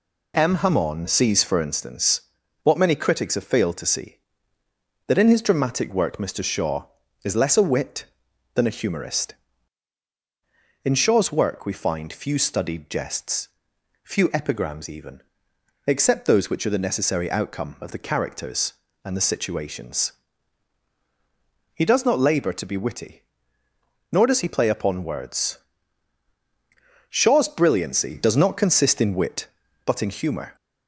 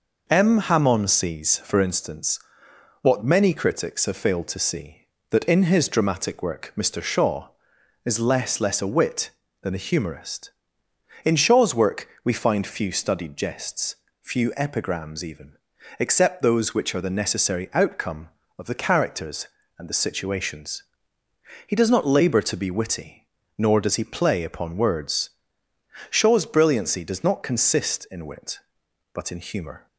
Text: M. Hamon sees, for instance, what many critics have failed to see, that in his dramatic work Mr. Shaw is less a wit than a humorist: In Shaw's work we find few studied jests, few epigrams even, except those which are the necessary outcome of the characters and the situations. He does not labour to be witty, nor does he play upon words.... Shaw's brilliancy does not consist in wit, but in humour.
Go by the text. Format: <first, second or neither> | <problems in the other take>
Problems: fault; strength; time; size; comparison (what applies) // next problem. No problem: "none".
first | says "less" twice; at 8.5 s // pauses between "work" and "we"; slight; at 12.0 s; 0.16 s long